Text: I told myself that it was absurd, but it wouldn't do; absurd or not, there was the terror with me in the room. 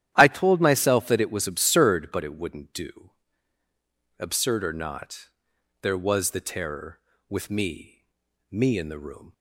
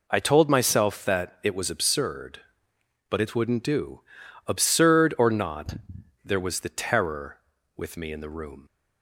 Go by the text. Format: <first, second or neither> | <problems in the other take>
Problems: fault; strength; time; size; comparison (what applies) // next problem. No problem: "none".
second | starts louder than the rest; strong; until 1.1 s; 11.5 dB // says "me" twice; at 8.5 s